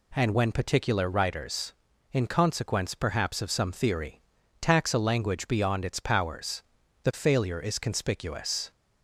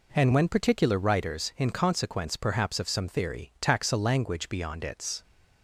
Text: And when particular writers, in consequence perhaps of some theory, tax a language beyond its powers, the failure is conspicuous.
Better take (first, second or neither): first